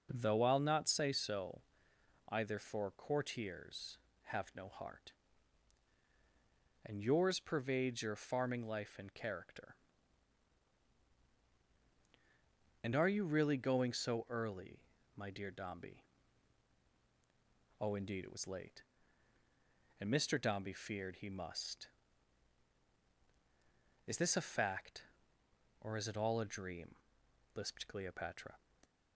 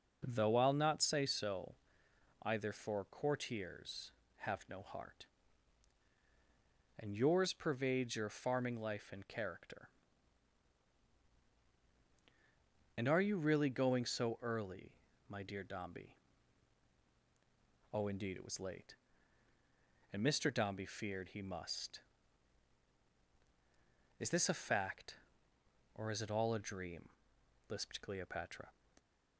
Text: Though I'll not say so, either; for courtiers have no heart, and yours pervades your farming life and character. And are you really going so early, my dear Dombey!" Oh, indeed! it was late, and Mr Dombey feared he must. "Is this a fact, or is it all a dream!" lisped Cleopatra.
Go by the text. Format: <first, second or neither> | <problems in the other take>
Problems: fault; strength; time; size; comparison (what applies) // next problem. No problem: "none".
neither | none